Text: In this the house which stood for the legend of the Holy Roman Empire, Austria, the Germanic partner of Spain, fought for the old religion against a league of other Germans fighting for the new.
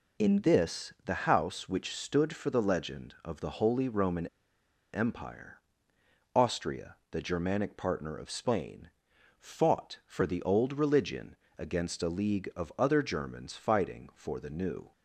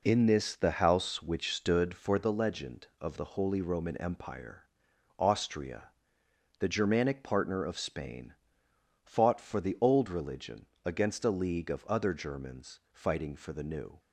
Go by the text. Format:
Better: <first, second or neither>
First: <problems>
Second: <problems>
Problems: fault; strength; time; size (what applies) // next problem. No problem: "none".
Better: second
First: pauses between "Roman" and "Empire"; noticeable; at 4.2 s; 0.66 s long // pauses between "religion" and "against"; slight; at 11.3 s; 0.22 s long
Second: pauses between "religion" and "against"; slight; at 10.6 s; 0.18 s long